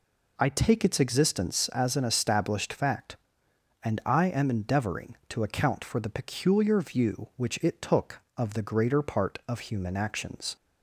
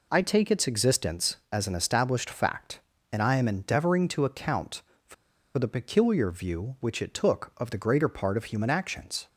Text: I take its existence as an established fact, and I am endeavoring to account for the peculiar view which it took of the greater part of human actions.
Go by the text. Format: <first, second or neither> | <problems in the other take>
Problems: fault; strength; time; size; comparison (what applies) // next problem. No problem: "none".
first | pauses between "for" and "the"; at 5.1 s; 0.42 s long